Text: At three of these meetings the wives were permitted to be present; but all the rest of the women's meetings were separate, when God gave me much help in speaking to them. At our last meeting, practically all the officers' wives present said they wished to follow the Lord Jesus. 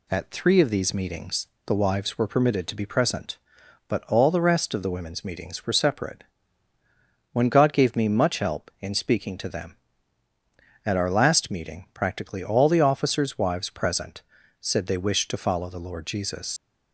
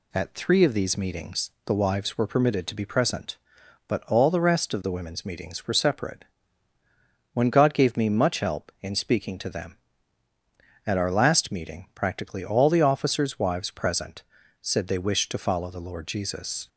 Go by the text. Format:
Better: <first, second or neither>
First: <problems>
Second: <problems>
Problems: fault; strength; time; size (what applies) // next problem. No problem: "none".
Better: second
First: pauses between "meetings" and "the"; slight; at 1.4 s; 0.20 s long // pauses between "present" and "said"; at 14.2 s; 0.38 s long // leaves "Jesus" unfinished; at 16.5 s; 110 ms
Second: pauses between "meetings" and "the"; slight; at 1.5 s; 0.16 s long // pauses between "present" and "said"; at 14.2 s; 0.38 s long